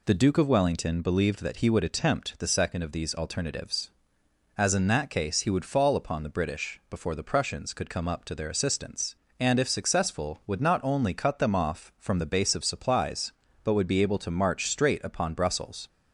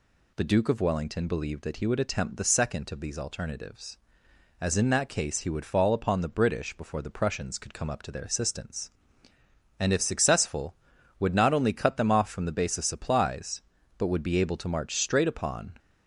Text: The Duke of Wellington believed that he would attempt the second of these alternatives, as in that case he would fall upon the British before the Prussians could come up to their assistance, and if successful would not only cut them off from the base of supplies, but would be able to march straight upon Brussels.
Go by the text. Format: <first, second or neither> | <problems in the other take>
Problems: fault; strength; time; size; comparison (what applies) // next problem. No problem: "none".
first | stops before "Brussels"; at 15.7 s